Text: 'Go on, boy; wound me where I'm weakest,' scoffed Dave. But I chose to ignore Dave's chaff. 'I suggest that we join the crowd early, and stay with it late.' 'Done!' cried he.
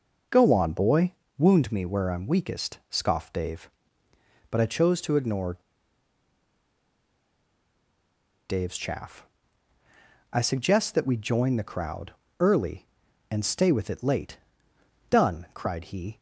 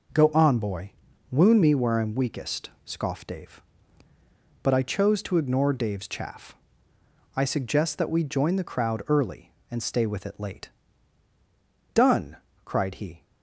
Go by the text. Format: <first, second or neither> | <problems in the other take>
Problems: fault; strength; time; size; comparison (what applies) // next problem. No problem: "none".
second | pauses between "ignore" and "Dave's"; strong; at 5.5 s; 2.9 s long // pauses between "crowd" and "early"; slight; at 12.1 s; 0.26 s long